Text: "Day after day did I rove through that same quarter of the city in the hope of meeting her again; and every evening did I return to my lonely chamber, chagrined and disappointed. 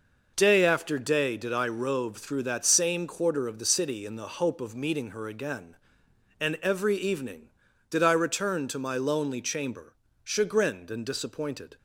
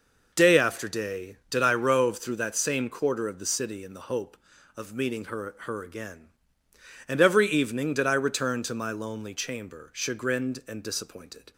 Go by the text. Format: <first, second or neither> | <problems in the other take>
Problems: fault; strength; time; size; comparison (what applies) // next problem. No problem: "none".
first | says "her" twice; at 5.5 s